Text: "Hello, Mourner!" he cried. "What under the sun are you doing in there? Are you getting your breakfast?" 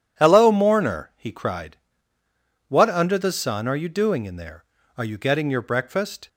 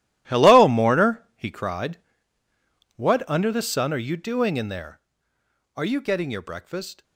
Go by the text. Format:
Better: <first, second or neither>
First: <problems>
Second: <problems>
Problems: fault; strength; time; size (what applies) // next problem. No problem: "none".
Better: first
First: none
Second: gets quieter; strong; throughout; 15 dB